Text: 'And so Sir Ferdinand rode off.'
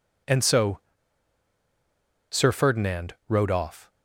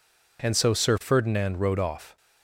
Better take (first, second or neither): second